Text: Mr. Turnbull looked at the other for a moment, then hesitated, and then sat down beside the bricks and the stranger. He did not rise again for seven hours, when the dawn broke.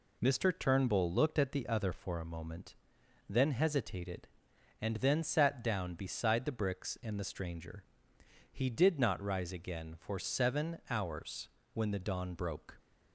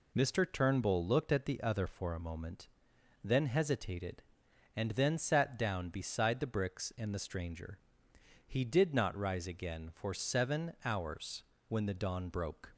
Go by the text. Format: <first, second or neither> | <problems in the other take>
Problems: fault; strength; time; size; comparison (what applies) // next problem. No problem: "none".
neither | none